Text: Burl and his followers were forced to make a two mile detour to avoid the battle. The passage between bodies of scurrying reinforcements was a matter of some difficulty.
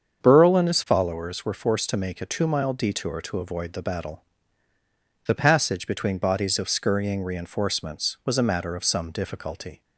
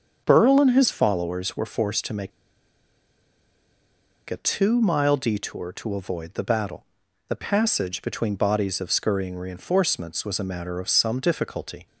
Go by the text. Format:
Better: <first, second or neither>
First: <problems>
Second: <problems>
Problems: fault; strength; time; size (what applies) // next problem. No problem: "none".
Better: first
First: starts louder than the rest; strong; until 1.2 s; 7 dB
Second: starts louder than the rest; strong; until 1.2 s; 7 dB // pauses between "make" and "a"; strong; at 2.3 s; 1.9 s long